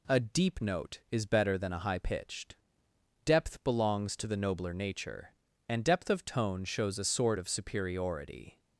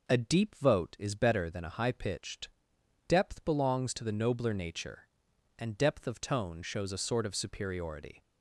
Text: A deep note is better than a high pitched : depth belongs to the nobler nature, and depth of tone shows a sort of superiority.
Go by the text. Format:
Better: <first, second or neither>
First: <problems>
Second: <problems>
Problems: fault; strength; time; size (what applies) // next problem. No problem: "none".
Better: first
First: none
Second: says "vote" for "note"; at 0.5 s